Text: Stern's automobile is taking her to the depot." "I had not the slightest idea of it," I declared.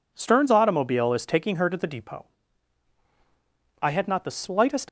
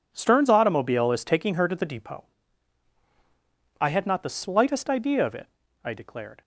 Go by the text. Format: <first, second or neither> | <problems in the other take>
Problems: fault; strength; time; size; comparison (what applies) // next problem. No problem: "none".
second | stops before "idea of it I declared"; at 4.8 s